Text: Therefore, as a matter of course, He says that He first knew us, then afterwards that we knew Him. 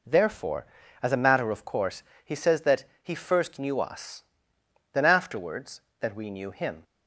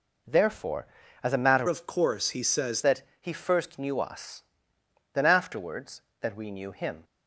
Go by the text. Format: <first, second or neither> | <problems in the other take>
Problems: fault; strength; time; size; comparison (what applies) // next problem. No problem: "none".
first | changes voice from "of" to "says"; from 1.6 to 2.8 s; 1.2 s long // pauses between "that" and "He"; slight; at 3.0 s; 0.18 s long; slight in the first